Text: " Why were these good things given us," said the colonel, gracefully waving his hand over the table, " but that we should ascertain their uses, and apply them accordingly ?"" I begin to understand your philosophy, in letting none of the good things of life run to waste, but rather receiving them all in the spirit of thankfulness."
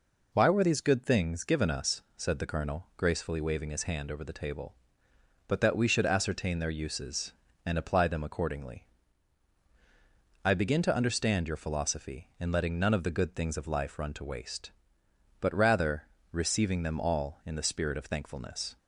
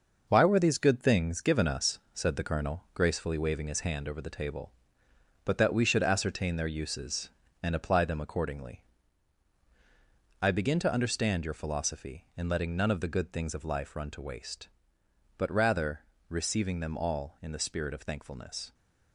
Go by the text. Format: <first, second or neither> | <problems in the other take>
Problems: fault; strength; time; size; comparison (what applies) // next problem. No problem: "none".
first | gets quieter; noticeable; throughout; 5.5 dB // pauses between "rather" and "receiving"; slight; at 16.0 s; 0.24 s long; slight in the first